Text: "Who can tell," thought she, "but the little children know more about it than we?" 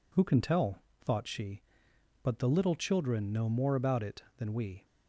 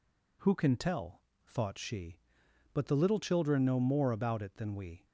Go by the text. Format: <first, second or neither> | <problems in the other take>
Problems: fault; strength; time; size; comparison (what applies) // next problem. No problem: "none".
neither | none